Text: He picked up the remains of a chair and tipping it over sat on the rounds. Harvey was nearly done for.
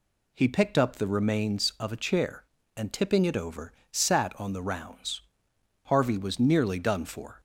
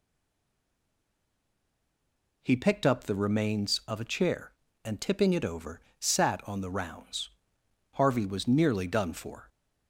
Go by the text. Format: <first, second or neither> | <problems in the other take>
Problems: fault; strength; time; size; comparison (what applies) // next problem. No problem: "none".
first | stays silent before the first word; until 2.4 s; 2.4 s long // pauses between "over" and "sat"; slight; at 5.8 s; 0.20 s long; slight in the first